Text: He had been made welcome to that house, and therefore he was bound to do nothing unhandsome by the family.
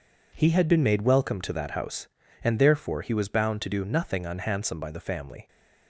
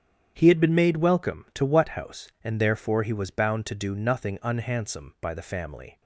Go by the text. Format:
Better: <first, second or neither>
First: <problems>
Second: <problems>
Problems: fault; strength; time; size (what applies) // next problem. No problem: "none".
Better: first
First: none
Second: starts louder than the rest; strong; until 1.3 s; 9 dB // says "what" for "that"; at 1.6 s